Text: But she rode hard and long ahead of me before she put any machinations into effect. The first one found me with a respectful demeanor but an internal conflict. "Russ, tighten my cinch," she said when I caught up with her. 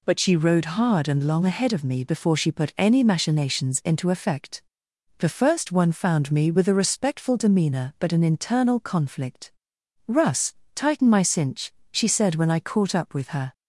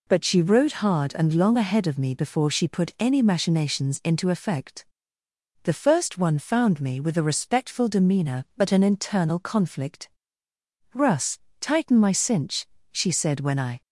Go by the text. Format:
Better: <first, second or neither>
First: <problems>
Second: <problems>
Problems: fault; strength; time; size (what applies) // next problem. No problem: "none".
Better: first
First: none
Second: stops before "caught up with her"; at 13.8 s